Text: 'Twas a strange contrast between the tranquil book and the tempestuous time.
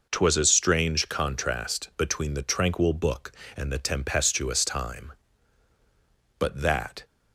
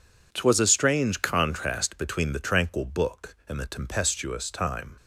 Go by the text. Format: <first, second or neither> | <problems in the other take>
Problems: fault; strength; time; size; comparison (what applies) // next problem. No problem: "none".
second | goes on to say "But that"; noticeable; from 6.3 s on; 0.68 s long